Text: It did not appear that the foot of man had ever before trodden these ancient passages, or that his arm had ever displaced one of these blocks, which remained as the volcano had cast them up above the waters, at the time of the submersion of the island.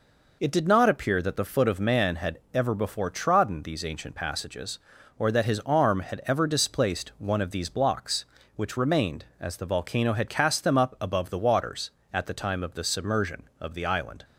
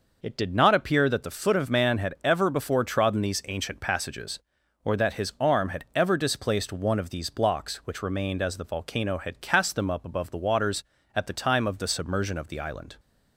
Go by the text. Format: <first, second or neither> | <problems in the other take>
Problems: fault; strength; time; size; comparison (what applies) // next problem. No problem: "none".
neither | none